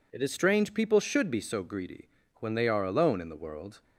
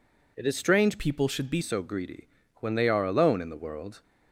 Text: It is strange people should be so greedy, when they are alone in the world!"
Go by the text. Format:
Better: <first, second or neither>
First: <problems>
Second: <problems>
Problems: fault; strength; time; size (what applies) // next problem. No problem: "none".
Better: first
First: none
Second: changes voice from "people" to "be"; from 0.9 to 1.6 s; 0.7 s long